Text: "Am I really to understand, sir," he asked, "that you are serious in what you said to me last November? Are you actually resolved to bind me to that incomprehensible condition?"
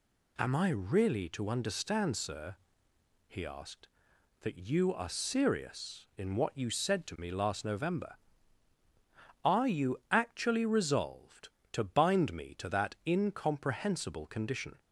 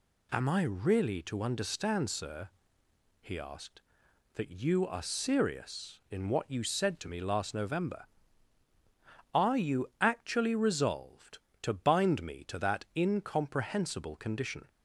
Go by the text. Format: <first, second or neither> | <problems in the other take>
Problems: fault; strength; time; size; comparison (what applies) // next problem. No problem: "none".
neither | none